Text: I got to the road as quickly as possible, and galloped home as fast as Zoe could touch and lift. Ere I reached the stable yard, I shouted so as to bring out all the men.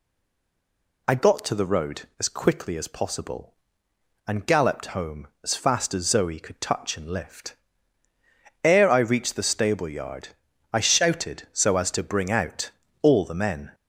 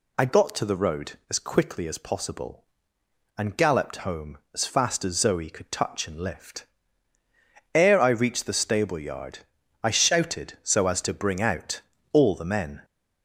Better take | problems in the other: second | stays silent before the first word; until 1.0 s; 1.0 s long // pauses between "out" and "all"; slight; at 12.7 s; 0.32 s long; slight in the second

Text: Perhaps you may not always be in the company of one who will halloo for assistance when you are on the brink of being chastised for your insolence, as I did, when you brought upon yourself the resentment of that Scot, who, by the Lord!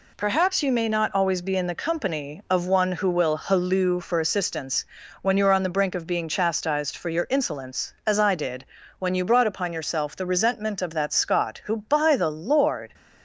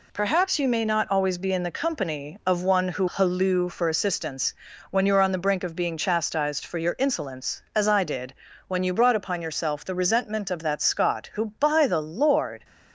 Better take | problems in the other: first | skips "will"; at 3.0 s // pauses between "assistance" and "when"; at 4.5 s; 0.38 s long; also in the first

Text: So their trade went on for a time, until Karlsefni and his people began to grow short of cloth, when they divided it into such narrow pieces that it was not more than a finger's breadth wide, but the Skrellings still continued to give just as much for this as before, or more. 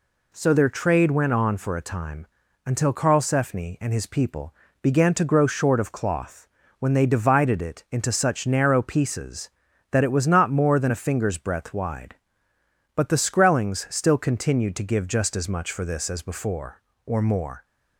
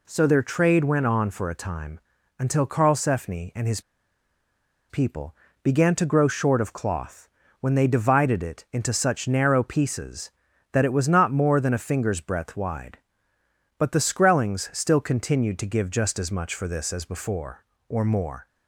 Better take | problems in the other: first | pauses between "his" and "people"; at 3.7 s; 1.0 s long // pauses between "people" and "began"; slight; at 5.3 s; 0.28 s long; slight in the first

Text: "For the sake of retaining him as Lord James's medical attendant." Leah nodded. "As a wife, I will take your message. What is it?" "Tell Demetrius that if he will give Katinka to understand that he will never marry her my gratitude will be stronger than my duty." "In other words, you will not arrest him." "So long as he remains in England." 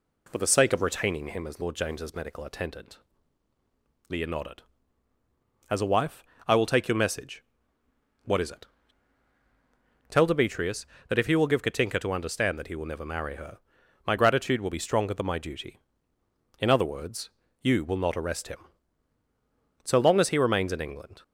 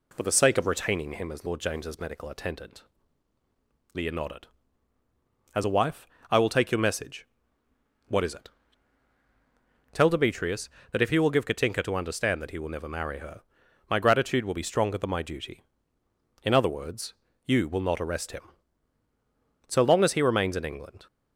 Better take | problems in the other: neither | pauses between "her" and "my"; noticeable; the same in both

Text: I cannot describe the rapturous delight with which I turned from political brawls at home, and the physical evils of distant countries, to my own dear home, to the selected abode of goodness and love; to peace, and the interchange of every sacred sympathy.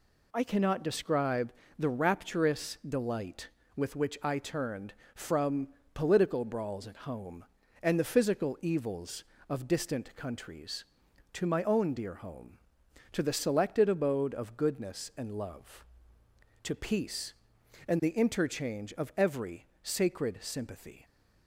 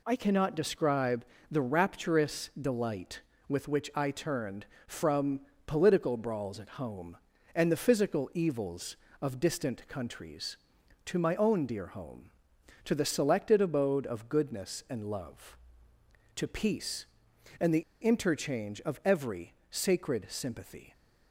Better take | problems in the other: first | pauses between "describe" and "the"; slight; at 1.2 s; 0.24 s long; slight in the first // pauses between "from" and "political"; slight; at 5.4 s; 0.24 s long; slight in the first // pauses between "the" and "interchange"; slight; at 17.8 s; 0.20 s long // pauses between "every" and "sacred"; slight; at 19.5 s; 0.16 s long; slight in the first

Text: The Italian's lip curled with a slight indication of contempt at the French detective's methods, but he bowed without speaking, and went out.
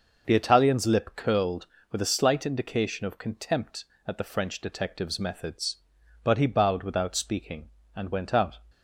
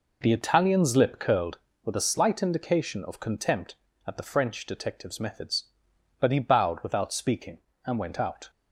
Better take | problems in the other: neither | none

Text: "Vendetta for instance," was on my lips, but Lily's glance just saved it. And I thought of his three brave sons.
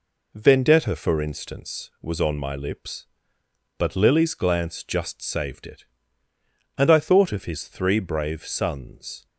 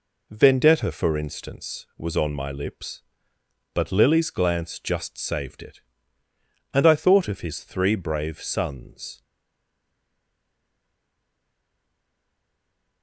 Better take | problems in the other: first | stays silent after the last word; strong; from 9.2 s on; 3.8 s long

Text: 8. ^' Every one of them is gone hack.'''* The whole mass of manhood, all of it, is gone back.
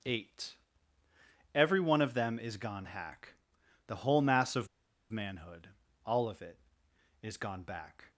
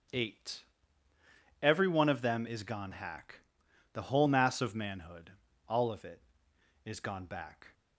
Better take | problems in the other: second | pauses between "of" and "manhood"; at 4.6 s; 0.42 s long

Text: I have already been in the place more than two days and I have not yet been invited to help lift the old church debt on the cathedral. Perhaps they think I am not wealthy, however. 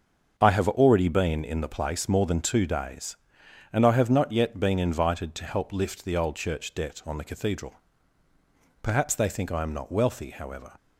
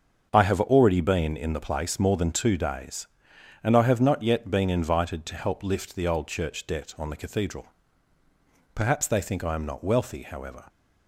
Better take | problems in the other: neither | starts louder than the rest; the same in both

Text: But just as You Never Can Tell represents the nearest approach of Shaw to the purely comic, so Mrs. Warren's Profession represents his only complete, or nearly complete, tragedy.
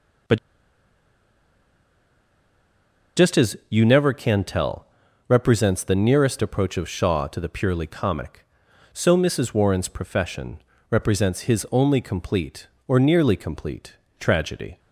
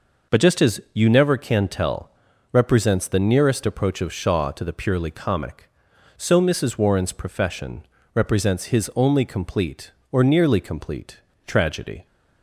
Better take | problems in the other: second | pauses between "But" and "just"; strong; at 0.3 s; 2.7 s long // pauses between "Tell" and "represents"; at 4.8 s; 0.42 s long; also in the second // pauses between "Profession" and "represents"; slight; at 10.6 s; 0.30 s long; slight in the second

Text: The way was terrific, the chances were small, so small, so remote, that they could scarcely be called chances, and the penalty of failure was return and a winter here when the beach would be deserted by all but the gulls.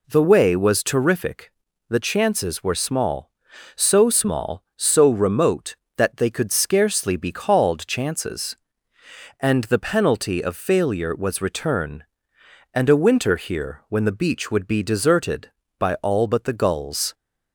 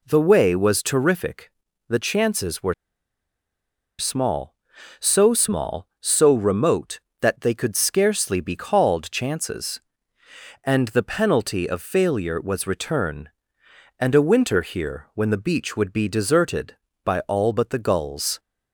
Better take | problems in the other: first | pauses between "were" and "small"; strong; at 2.7 s; 1.2 s long

